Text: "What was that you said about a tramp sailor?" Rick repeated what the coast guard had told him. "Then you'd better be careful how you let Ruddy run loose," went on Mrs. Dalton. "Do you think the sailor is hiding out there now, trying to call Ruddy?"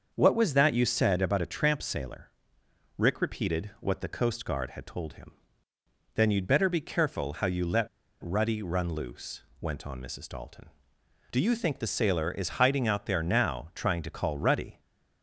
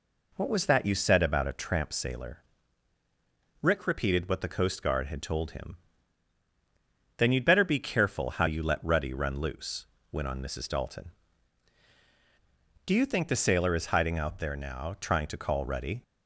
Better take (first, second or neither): second